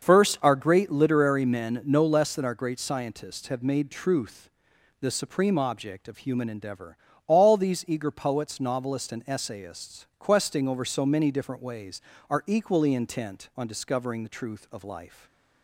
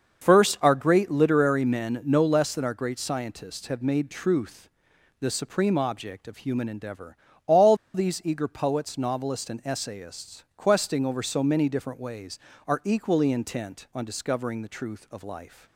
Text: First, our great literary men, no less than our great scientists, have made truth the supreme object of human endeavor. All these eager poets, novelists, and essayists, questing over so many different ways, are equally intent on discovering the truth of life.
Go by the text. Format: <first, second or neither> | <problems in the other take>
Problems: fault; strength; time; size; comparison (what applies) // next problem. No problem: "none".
first | starts louder than the rest; until 1.2 s; 6.5 dB; also in the first // pauses between "truth" and "the"; noticeable; at 4.6 s; 0.50 s long; noticeable in the first // pauses between "All" and "these"; slight; at 7.7 s; 0.19 s long